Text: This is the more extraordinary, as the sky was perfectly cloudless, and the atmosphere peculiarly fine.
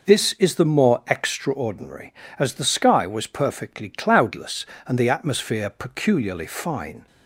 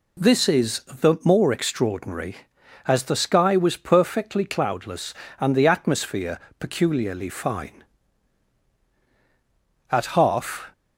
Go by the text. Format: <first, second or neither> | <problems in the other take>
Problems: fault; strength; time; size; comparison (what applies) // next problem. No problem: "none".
first | pauses between "atmosphere" and "peculiarly"; slight; at 6.3 s; 0.18 s long // goes on to say "At half"; noticeable; from 9.9 s on; 0.80 s long